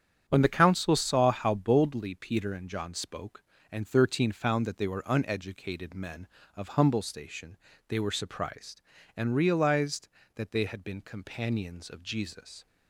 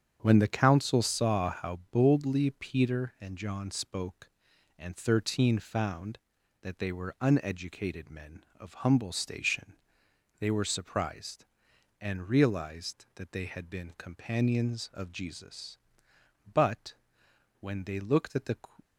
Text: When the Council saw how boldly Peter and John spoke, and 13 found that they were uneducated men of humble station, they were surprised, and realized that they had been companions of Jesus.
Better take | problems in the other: first | starts louder than the rest; strong; until 1.2 s; 7.5 dB; strong in the first // goes on to say "But when they looked at the"; strong; from 16.5 s on; 2.0 s long

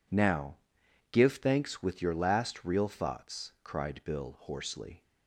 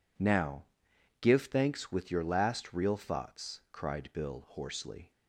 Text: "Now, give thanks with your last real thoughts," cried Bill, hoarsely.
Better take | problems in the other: neither | none

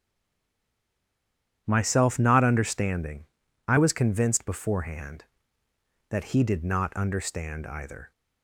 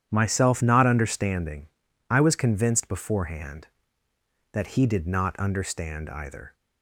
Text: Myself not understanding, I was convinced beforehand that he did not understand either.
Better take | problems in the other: second | stays silent before the first word; noticeable; until 1.6 s; 1.6 s long // starts louder than the rest; strong; until 2.6 s; 9.5 dB; strong in the second

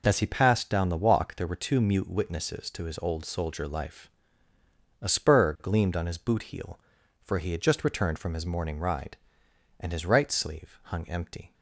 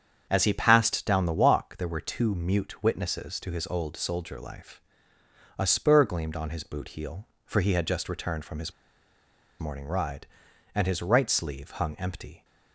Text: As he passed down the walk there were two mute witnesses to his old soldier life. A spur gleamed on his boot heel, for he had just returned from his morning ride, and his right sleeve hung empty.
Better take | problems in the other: first | starts louder than the rest; strong; until 1.3 s; 7.5 dB // pauses between "his" and "morning"; noticeable; at 8.7 s; 0.87 s long

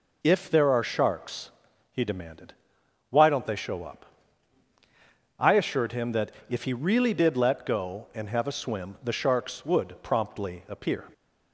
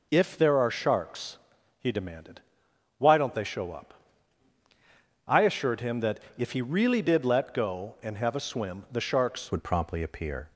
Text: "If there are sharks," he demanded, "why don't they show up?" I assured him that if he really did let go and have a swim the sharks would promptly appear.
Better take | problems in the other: first | pauses between "that" and "if"; slight; at 6.1 s; 0.20 s long; slight in the first // changes voice at "would"; from 9.5 s on; 0.9 s long

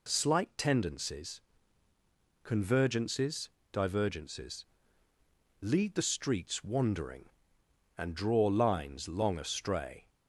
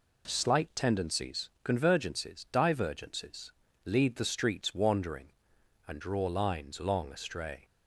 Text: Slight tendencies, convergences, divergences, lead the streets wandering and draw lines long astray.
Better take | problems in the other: neither | none

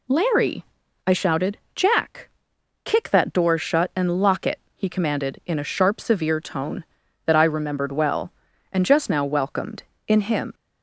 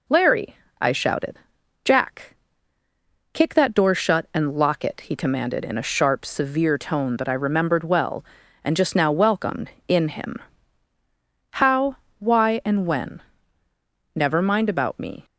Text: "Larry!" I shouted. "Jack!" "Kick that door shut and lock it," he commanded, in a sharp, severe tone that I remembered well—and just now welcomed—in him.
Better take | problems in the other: first | goes on to say "How why and when Never mind about me"; strong; from 11.5 s on; 3.7 s long

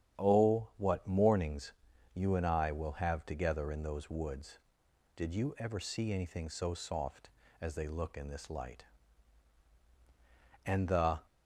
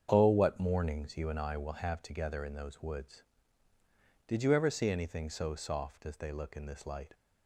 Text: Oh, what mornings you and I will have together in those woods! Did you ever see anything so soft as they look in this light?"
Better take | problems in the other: second | starts louder than the rest; strong; until 1.2 s; 8.5 dB; strong in the second // pauses between "mornings" and "you"; at 1.7 s; 0.42 s long // goes on to say "And the"; from 10.6 s on; 0.54 s long

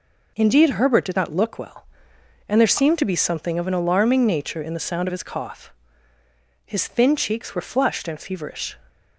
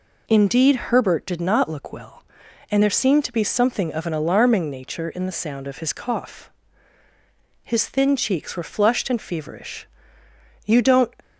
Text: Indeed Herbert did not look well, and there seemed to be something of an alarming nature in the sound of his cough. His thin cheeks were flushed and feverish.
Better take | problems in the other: first | goes on to say "You don't"; slight; from 10.6 s on; 0.48 s long

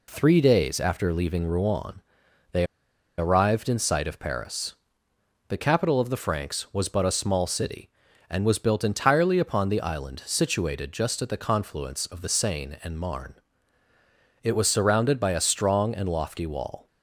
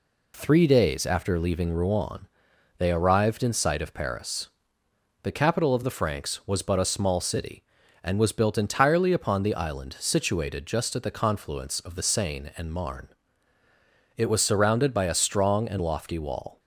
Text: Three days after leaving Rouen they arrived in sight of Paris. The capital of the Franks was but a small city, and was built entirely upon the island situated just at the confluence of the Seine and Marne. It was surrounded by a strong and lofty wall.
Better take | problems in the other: second | pauses between "Rouen" and "they"; noticeable; at 2.0 s; 0.50 s long; noticeable in the second // pauses between "they" and "arrived"; noticeable; at 2.6 s; 0.52 s long

